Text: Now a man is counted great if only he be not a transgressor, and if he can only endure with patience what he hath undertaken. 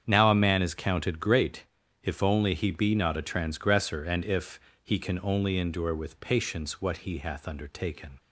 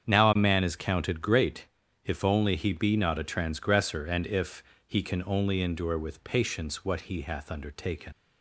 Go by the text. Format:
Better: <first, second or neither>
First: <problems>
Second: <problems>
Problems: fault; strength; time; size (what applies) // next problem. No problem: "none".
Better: first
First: starts louder than the rest; strong; until 1.0 s; 8 dB // pauses between "great" and "if"; at 1.6 s; 0.38 s long // pauses between "if" and "he"; slight; at 4.5 s; 0.24 s long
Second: starts louder than the rest; strong; until 1.1 s; 8 dB // pauses between "great" and "if"; at 1.6 s; 0.38 s long // pauses between "if" and "he"; slight; at 4.6 s; 0.24 s long // leaves "undertaken" unfinished; at 8.1 s; 110 ms